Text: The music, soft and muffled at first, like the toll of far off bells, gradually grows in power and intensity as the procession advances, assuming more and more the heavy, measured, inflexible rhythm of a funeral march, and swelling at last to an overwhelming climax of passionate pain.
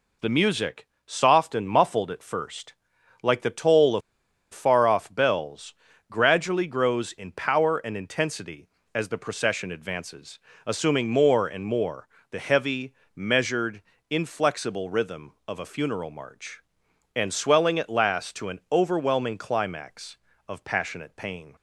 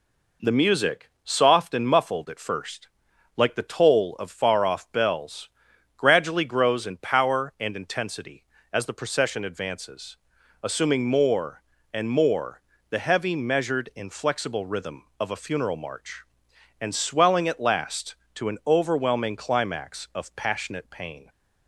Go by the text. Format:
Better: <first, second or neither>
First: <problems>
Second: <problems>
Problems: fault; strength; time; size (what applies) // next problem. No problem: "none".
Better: second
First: pauses between "of" and "far"; noticeable; at 4.0 s; 0.52 s long // pauses between "more" and "the"; slight; at 12.0 s; 0.22 s long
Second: pauses between "more" and "the"; slight; at 12.6 s; 0.26 s long